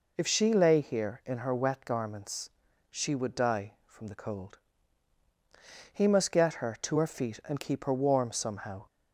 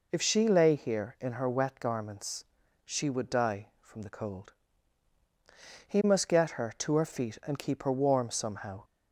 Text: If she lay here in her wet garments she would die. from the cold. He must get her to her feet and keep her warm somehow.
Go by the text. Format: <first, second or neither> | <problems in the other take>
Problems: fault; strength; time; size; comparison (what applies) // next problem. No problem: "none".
neither | pauses between "garments" and "she"; the same in both